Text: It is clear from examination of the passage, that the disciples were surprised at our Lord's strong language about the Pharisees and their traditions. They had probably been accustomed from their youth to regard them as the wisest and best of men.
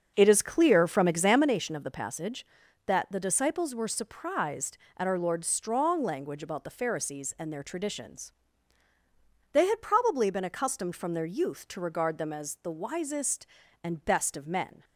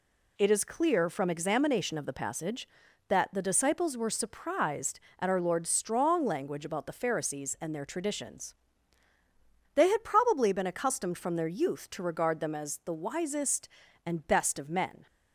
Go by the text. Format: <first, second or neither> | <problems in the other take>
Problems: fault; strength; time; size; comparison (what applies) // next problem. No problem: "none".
second | starts louder than the rest; until 1.6 s; 6.5 dB